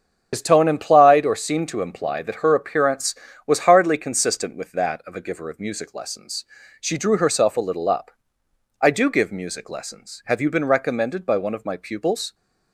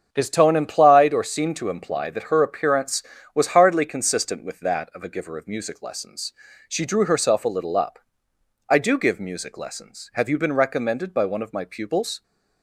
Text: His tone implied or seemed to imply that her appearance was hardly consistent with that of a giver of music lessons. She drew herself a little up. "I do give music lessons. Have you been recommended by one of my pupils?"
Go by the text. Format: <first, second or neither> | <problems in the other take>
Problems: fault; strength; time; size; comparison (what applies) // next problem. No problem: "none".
second | loses the start of "His"; at 0.3 s; 80 ms // starts louder than the rest; strong; until 1.3 s; 7.5 dB; strong in the second